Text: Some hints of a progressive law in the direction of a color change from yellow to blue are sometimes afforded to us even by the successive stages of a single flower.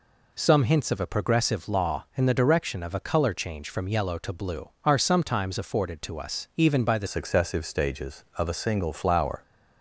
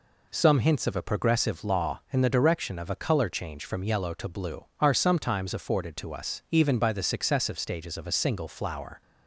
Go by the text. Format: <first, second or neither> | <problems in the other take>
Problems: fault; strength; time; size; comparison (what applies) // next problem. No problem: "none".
second | changes voice at "successive"; from 7.0 s on; 2.4 s long